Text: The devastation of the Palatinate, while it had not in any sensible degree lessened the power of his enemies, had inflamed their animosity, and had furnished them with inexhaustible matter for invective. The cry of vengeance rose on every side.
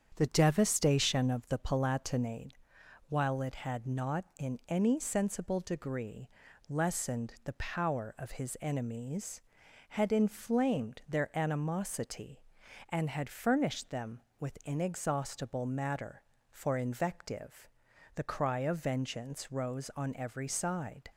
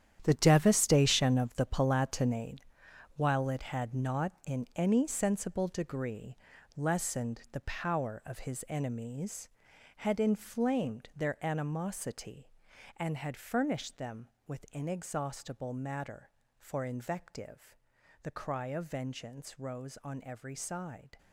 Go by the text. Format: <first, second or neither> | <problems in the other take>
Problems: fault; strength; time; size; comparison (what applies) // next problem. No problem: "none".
first | gets quieter; strong; throughout; 12.5 dB // starts louder than the rest; strong; until 1.2 s; 9.5 dB; strong in the first // pauses between "degree" and "lessened"; at 6.3 s; 0.40 s long; also in the first